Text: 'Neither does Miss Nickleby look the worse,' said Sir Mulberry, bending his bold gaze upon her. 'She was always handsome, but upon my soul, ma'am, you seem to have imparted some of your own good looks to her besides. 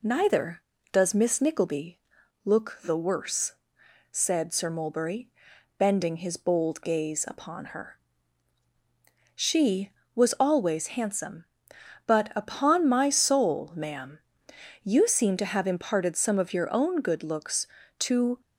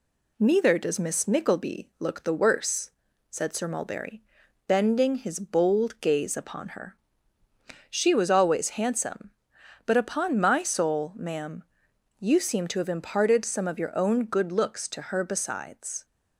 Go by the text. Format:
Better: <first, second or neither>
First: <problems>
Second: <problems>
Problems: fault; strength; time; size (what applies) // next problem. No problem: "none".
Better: second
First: pauses between "Nickleby" and "look"; noticeable; at 2.0 s; 0.46 s long // stops before "her besides"; at 18.4 s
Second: none